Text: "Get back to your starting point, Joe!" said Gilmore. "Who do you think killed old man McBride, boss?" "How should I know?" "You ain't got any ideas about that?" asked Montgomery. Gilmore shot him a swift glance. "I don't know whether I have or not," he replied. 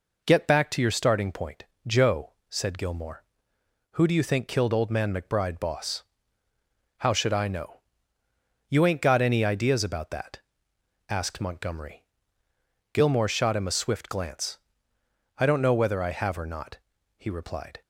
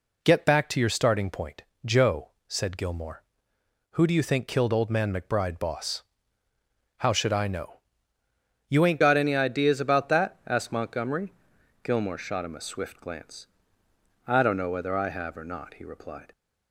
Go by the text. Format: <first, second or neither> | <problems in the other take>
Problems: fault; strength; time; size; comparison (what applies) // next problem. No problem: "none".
first | changes voice at "got"; from 9.0 s on; 7.3 s long